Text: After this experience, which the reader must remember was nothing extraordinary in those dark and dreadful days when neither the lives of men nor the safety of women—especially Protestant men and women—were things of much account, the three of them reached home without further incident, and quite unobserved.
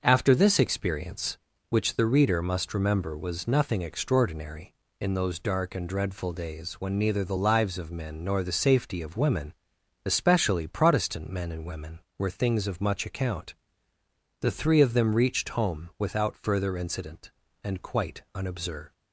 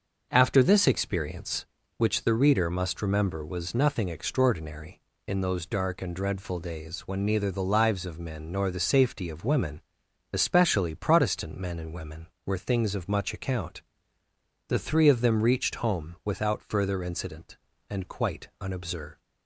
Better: neither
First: starts louder than the rest; until 1.0 s; 6.5 dB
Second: starts louder than the rest; until 1.3 s; 6.5 dB

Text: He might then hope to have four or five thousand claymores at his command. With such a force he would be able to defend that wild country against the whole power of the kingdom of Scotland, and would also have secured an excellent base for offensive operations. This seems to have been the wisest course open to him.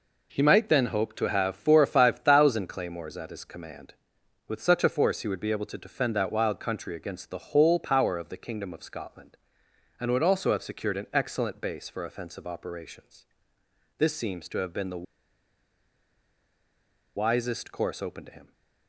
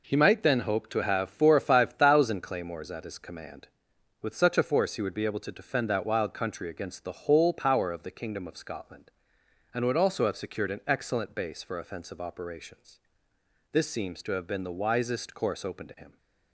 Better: second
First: pauses between "the" and "wisest"; strong; at 15.0 s; 2.1 s long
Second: none

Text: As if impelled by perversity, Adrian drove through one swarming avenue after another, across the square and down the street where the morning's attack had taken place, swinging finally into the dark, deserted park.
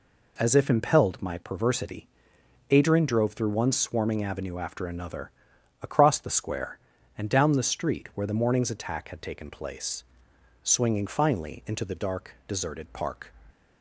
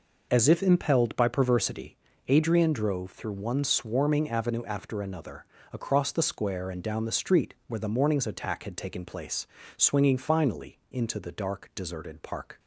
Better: second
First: says "my" for "by"; at 1.2 s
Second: none

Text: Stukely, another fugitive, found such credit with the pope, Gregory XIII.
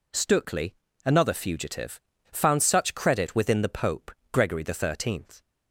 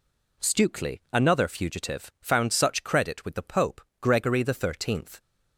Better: second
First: says "within" for "with"; at 3.3 s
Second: none

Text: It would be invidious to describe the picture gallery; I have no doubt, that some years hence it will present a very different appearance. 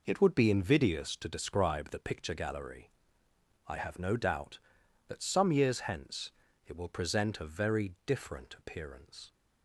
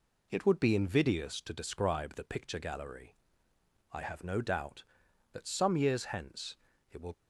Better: first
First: pauses between "hence" and "it"; slight; at 6.3 s; 0.34 s long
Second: pauses between "hence" and "it"; slight; at 6.5 s; 0.34 s long // stops before "present a very different appearance"; at 7.1 s

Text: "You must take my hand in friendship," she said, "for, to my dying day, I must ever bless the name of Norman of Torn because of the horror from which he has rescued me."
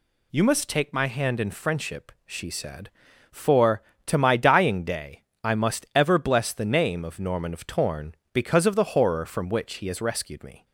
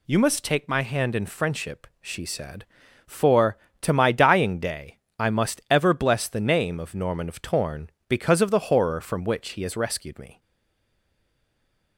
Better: first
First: none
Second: stays silent after the last word; noticeable; from 10.4 s on; 1.5 s long

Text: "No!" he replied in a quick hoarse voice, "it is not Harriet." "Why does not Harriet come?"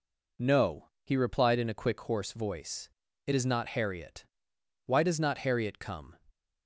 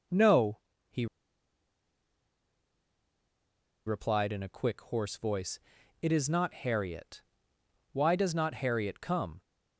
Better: first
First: none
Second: pauses between "he" and "replied"; strong; at 1.0 s; 2.7 s long

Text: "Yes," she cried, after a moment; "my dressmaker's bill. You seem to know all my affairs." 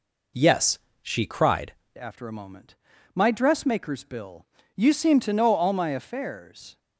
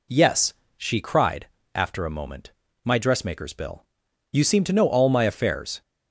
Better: second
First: changes voice at "after"; from 1.9 s on; 4.8 s long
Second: none

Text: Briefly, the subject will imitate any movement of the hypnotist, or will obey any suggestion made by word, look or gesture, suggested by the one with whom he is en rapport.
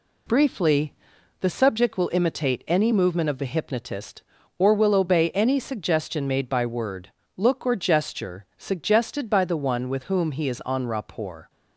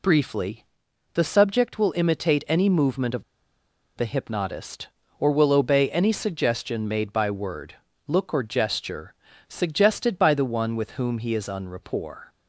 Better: first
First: none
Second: pauses between "of" and "the"; noticeable; at 3.2 s; 0.73 s long

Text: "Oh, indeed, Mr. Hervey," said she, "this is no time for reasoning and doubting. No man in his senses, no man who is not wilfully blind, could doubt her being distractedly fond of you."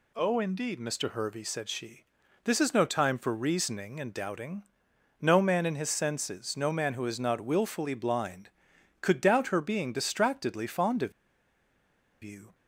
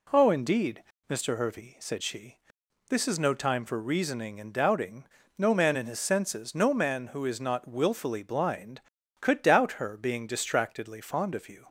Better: second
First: pauses between "of" and "you"; at 11.1 s; 1.1 s long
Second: none

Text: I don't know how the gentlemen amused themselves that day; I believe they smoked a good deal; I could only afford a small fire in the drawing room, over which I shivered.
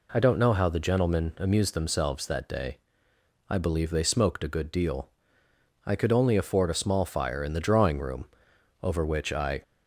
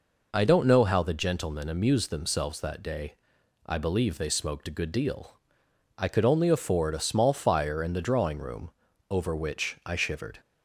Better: second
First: stops before "shivered"; at 9.6 s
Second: none

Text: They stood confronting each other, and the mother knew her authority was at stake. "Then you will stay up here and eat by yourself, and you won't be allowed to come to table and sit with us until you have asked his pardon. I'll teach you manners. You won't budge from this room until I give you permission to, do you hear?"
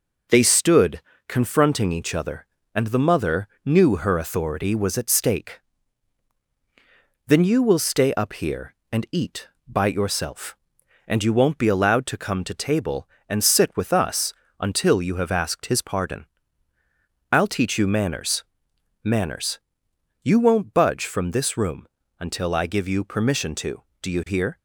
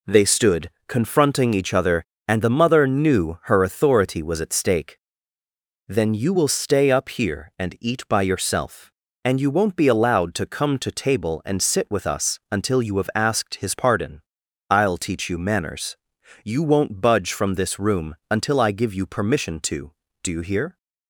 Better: second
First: pauses between "stood" and "confronting"; slight; at 1.0 s; 0.26 s long // pauses between "mother" and "knew"; slight; at 3.4 s; 0.16 s long // pauses between "us" and "until"; slight; at 14.3 s; 0.26 s long // says "manners" twice; at 19.0 s // pauses between "room" and "until"; slight; at 21.8 s; 0.34 s long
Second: pauses between "stood" and "confronting"; slight; at 0.7 s; 0.16 s long

